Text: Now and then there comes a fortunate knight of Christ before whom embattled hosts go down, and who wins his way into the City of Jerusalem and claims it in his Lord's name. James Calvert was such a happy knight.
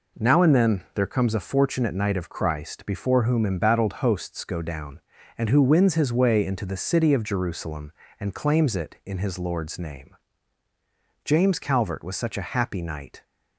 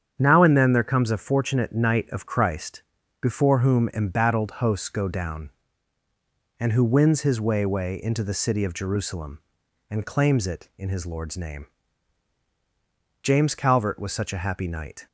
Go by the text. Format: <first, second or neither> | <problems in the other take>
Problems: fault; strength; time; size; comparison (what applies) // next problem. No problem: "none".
first | starts louder than the rest; strong; until 1.1 s; 8.5 dB // pauses between "Christ" and "before"; at 2.8 s; 0.40 s long // says "way" twice; at 7.6 s